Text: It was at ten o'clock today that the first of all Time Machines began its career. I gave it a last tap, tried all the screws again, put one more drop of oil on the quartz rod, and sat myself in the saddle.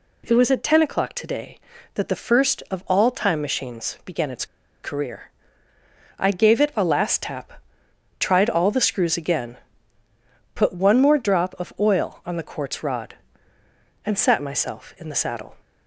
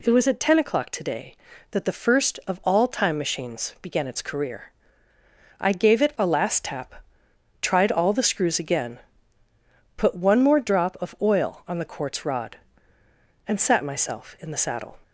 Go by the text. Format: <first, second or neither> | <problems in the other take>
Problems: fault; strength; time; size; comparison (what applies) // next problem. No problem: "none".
second | pauses between "its" and "career"; at 4.4 s; 0.36 s long